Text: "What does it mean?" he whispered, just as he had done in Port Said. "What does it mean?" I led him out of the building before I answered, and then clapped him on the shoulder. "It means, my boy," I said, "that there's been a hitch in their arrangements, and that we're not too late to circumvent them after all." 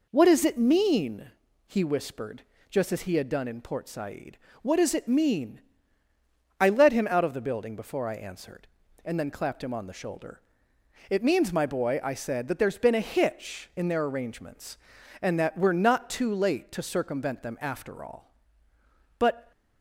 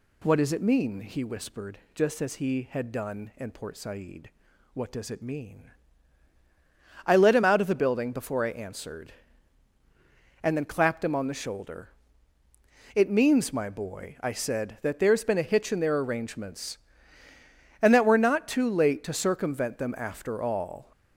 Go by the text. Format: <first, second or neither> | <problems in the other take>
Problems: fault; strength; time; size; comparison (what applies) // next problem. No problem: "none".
second | goes on to say "But"; slight; from 19.1 s on; 0.32 s long